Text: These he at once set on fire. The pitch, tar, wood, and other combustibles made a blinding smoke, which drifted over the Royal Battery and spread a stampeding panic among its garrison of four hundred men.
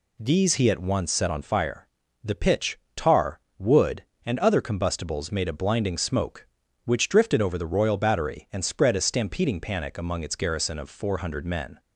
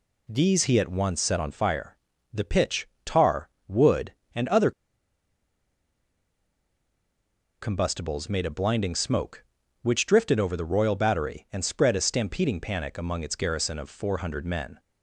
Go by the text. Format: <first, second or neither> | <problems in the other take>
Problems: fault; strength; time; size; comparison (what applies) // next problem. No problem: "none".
first | pauses between "other" and "combustibles"; strong; at 4.7 s; 2.9 s long